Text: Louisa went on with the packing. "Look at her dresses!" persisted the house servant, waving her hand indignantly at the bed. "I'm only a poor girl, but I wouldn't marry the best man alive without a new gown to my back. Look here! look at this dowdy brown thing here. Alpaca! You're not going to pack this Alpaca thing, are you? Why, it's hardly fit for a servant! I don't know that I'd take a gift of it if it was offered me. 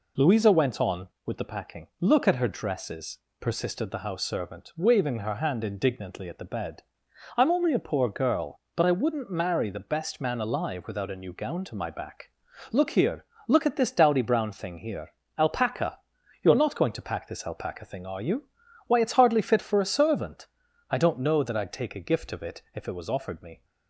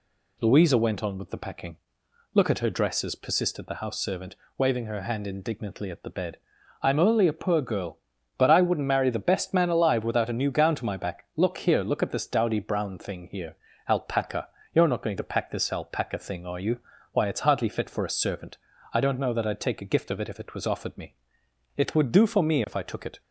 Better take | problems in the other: first | goes on to say "It would do for me if I took it"; from 21.7 s on; 1.4 s long

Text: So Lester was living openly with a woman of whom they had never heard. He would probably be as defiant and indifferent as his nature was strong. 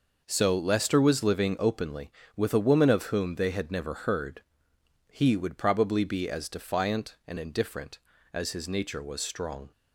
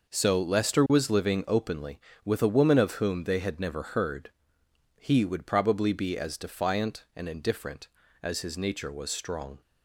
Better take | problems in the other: neither | none

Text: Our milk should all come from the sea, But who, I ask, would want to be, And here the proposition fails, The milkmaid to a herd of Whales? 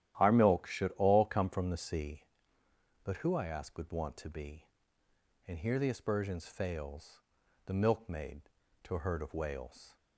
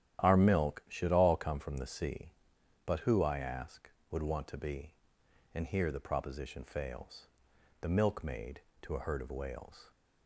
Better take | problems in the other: second | starts louder than the rest; strong; until 1.2 s; 12 dB; strong in the second // says "aspersions" for "proposition"; at 5.8 s

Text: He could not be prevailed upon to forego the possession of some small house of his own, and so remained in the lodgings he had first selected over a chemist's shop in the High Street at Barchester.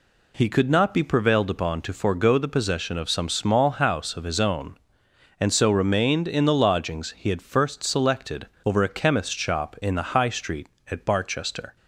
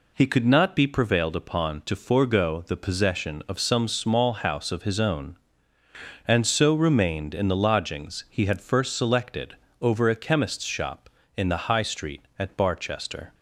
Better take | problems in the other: neither | pauses between "selected" and "over"; slight; the same in both

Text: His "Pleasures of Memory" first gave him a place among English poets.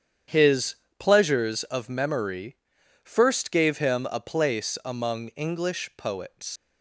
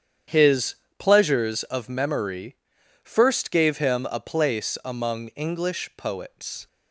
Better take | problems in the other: second | starts louder than the rest; strong; until 1.5 s; 8.5 dB; strong in the second // pauses between "His" and "Pleasures"; slight; at 0.7 s; 0.24 s long; slight in the second // pauses between "Memory" and "first"; noticeable; at 2.5 s; 0.48 s long; noticeable in the second // leaves "poets" unfinished; at 6.5 s; 110 ms

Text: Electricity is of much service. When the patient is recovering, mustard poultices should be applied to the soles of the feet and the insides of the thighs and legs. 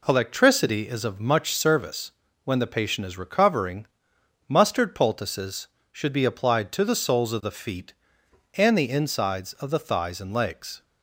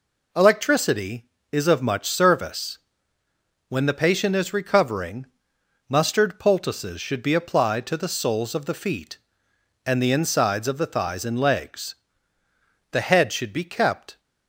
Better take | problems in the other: first | goes on to say "The head should be kept"; noticeable; from 12.9 s on; 1.2 s long

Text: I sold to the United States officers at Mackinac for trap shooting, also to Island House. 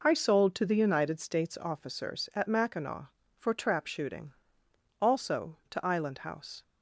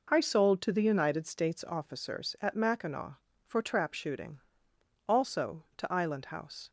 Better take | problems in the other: neither | none

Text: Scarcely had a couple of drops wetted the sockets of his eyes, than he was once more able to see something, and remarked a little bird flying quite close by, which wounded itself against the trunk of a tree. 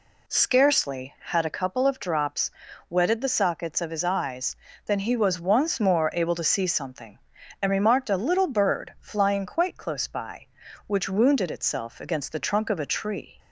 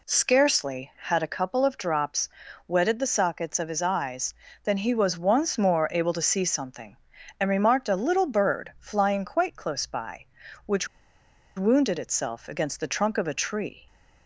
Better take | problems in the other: first | pauses between "drops" and "wetted"; at 2.2 s; 0.40 s long; also in the first // pauses between "which" and "wounded"; noticeable; at 10.8 s; 0.70 s long

